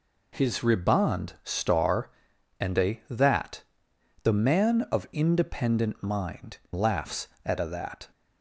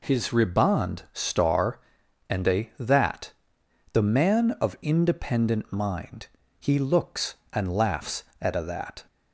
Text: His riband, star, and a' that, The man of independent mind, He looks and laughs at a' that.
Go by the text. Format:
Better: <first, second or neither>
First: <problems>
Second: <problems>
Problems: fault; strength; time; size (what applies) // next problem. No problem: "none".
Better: second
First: skips "He looks and"; at 6.6 s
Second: none